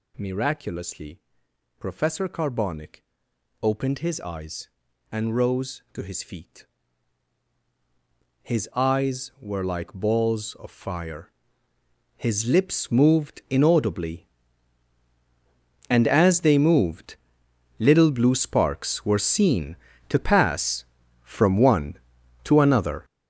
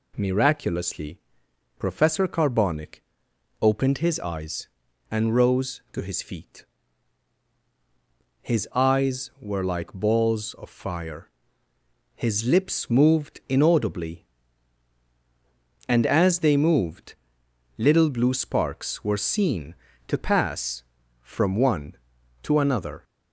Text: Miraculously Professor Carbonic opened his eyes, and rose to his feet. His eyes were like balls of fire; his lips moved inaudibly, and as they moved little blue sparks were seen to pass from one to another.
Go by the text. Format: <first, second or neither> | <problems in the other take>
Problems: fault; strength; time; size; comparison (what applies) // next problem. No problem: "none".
second | gets louder; strong; throughout; 10.5 dB // pauses between "Miraculously" and "Professor"; noticeable; at 1.1 s; 0.58 s long; noticeable in the second // pauses between "Carbonic" and "opened"; noticeable; at 3.0 s; 0.58 s long; noticeable in the second // pauses between "moved" and "little"; noticeable; at 17.1 s; 0.64 s long; noticeable in the second